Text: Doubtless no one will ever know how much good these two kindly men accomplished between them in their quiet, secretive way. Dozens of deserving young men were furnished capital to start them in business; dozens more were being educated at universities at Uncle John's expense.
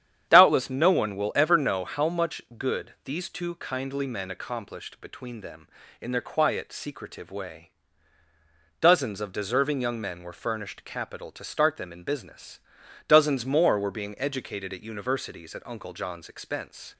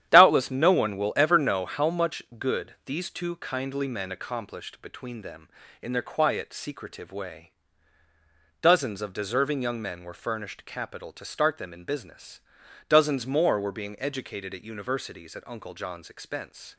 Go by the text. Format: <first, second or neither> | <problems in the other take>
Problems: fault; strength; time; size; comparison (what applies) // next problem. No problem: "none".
first | gets quieter; strong; throughout; 9 dB // starts louder than the rest; strong; until 1.1 s; 10.5 dB; strong in the first // pauses between "much" and "good"; slight; at 2.2 s; 0.16 s long; slight in the first